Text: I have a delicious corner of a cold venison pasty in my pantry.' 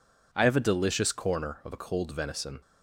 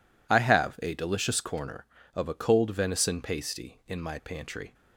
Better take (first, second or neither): second